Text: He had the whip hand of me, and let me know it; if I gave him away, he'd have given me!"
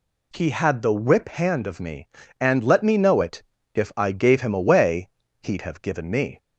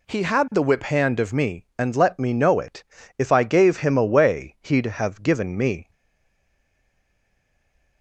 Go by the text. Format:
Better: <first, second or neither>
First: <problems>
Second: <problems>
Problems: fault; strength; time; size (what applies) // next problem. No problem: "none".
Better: first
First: none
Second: stays silent after the last word; from 5.9 s on; 2.1 s long